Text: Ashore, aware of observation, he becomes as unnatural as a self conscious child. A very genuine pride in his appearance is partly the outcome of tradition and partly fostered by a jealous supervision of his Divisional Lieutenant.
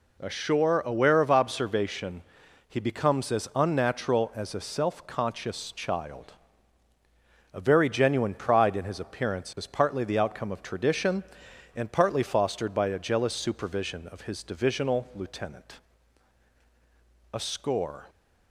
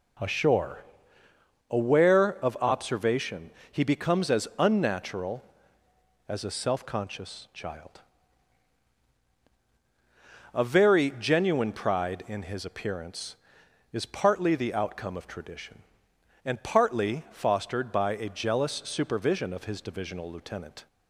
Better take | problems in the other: second | goes on to say "A score"; noticeable; from 17.3 s on; 0.74 s long

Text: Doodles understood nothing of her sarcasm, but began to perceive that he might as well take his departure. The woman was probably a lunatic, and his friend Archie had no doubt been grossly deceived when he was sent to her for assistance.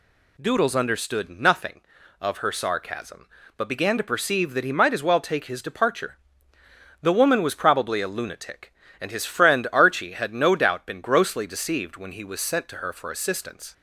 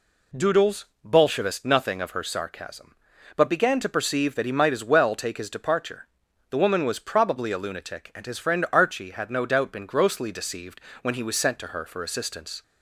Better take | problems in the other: first | says "bolshevist" for "understood"; at 1.0 s // pauses between "deceived" and "when"; slight; at 10.8 s; 0.22 s long

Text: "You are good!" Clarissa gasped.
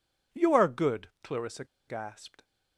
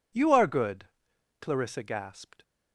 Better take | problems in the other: second | pauses between "Clarissa" and "gasped"; slight; at 1.6 s; 0.22 s long

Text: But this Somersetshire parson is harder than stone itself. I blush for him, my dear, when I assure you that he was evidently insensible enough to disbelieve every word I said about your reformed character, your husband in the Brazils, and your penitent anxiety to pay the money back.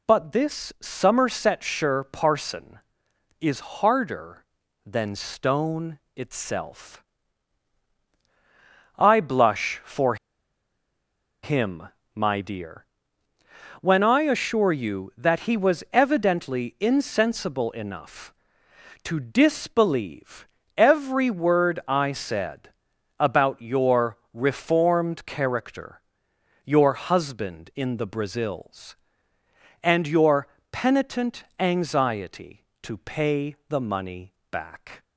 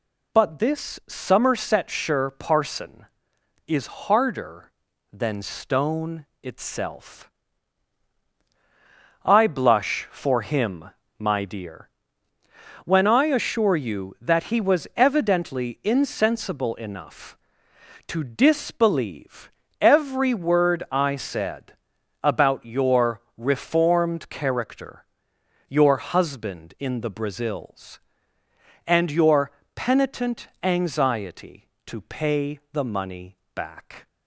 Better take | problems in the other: second | pauses between "stone" and "itself"; slight; at 5.9 s; 0.16 s long; slight in the second // pauses between "for" and "him"; strong; at 10.1 s; 1.2 s long // pauses between "disbelieve" and "every"; slight; at 20.4 s; 0.30 s long; slight in the second // pauses between "said" and "about"; noticeable; at 22.7 s; 0.48 s long; noticeable in the second // pauses between "your" and "reformed"; slight; at 24.1 s; 0.16 s long; slight in the second // pauses between "your" and "penitent"; slight; at 30.4 s; 0.24 s long; slight in the second // pauses between "money" and "back"; slight; at 34.3 s; 0.18 s long; slight in the second

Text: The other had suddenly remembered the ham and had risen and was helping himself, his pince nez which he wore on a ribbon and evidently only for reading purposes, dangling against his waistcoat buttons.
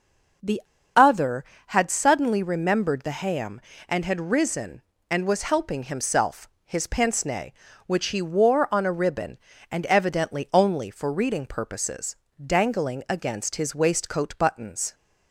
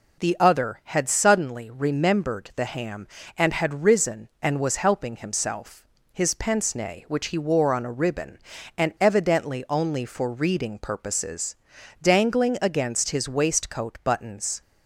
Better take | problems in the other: second | pauses between "The" and "other"; slight; at 0.6 s; 0.34 s long

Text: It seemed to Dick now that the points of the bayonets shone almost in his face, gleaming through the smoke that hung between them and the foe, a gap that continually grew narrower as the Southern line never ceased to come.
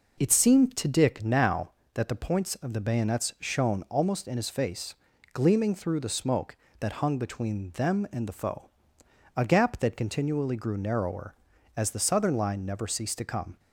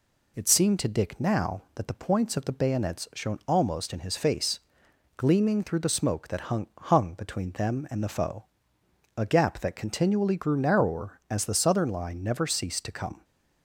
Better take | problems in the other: first | says "hung" twice; at 6.7 s

